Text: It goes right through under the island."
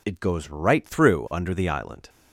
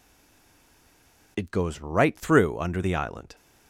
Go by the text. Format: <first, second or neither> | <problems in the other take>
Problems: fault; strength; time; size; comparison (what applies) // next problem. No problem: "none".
first | stays silent before the first word; noticeable; until 1.3 s; 1.3 s long